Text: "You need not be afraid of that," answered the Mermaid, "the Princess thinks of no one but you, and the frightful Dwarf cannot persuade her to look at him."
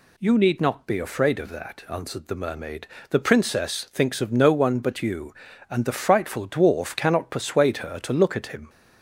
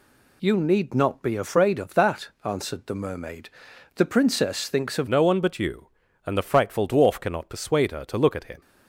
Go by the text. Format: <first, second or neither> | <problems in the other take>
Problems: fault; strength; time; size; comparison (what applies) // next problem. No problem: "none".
first | changes voice at "no"; from 5.0 s on; 3.6 s long